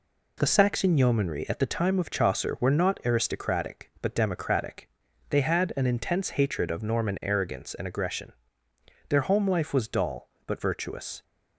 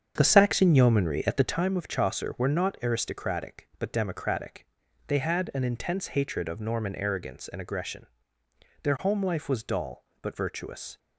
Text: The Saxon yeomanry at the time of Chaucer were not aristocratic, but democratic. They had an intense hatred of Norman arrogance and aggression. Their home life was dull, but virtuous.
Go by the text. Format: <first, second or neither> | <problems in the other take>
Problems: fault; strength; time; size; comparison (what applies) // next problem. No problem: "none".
first | starts louder than the rest; strong; until 1.7 s; 7.5 dB